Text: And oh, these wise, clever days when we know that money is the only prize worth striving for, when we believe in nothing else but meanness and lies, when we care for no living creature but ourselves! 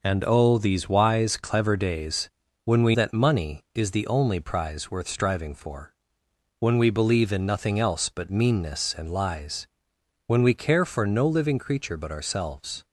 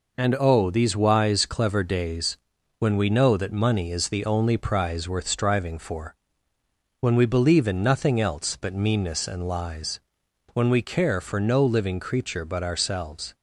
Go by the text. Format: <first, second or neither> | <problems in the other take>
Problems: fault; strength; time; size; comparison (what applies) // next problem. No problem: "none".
second | pauses between "days" and "when"; slight; at 2.2 s; 0.34 s long; also in the second // skips "know"; at 2.9 s